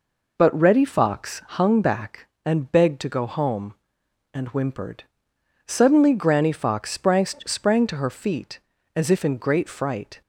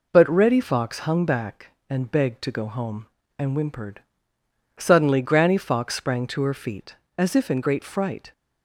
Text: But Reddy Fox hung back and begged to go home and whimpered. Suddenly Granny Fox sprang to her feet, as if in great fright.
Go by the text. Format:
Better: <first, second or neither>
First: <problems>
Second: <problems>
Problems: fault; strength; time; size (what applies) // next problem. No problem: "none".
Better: second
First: says "sprang" twice; at 7.2 s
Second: none